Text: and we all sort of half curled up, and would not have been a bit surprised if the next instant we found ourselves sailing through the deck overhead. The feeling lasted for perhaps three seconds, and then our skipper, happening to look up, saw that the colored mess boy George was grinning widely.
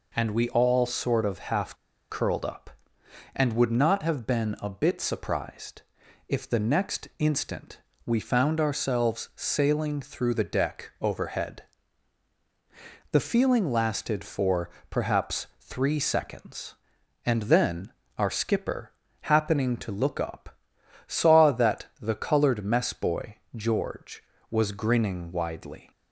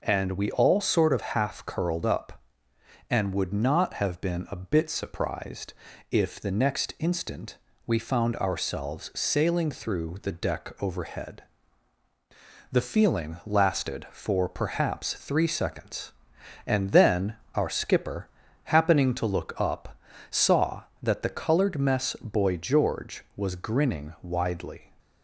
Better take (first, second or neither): second